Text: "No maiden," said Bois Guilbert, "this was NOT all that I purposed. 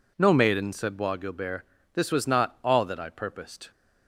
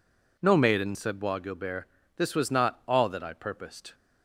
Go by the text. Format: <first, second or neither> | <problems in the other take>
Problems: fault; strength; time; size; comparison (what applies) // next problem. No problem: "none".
neither | none